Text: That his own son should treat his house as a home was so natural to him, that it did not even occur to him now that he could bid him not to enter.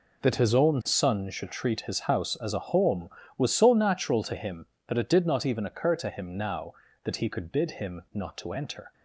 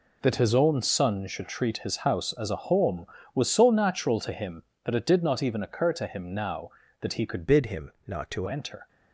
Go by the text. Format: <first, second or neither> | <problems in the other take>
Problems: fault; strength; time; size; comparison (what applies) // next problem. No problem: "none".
first | changes voice from "bid" to "to"; from 7.4 to 8.4 s; 1.0 s long // pauses between "him" and "not"; slight; at 7.9 s; 0.16 s long